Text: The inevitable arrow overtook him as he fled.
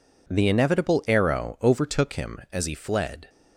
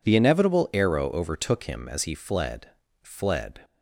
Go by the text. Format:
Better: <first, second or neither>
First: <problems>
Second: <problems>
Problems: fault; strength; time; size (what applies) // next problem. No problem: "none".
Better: first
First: none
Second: says "fled" twice; at 3.0 s